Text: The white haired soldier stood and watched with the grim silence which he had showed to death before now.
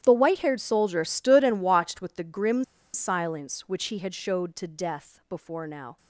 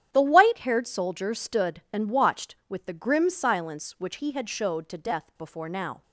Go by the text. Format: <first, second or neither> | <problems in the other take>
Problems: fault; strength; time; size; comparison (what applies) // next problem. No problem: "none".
second | starts louder than the rest; strong; until 1.0 s; 11 dB; strong in the second // pauses between "grim" and "silence"; slight; at 2.6 s; 0.30 s long